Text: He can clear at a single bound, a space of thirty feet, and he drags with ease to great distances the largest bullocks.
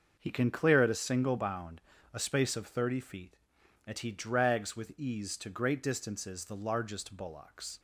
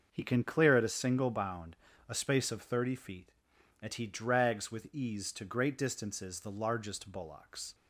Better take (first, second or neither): neither